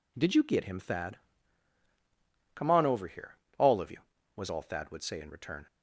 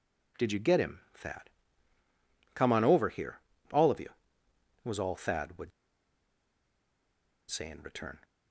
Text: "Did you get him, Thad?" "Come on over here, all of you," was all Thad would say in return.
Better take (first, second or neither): first